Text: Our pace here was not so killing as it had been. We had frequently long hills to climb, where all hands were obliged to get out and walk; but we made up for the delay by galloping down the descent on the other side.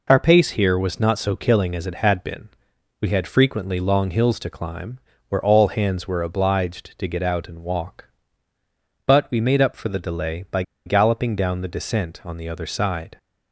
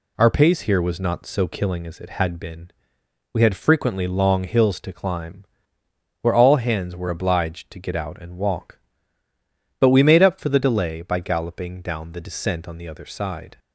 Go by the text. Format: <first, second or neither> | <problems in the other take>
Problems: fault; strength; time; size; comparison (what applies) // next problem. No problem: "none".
second | pauses between "by" and "galloping"; slight; at 10.6 s; 0.23 s long